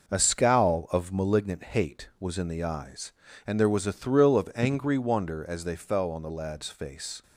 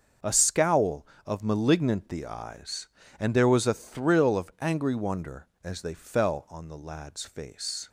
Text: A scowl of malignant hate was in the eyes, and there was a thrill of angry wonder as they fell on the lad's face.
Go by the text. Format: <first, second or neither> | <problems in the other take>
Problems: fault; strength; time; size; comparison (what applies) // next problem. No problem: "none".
first | starts louder than the rest; until 1.4 s; 6.5 dB // skips "hate was in"; at 2.0 s